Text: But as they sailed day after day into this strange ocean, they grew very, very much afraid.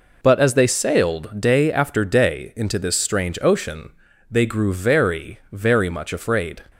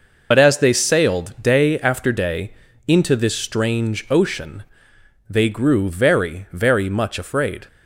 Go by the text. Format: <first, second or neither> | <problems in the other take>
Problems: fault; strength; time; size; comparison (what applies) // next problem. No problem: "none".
first | loses the start of "But"; at 0.3 s; 55 ms // pauses between "day" and "into"; slight; at 2.5 s; 0.36 s long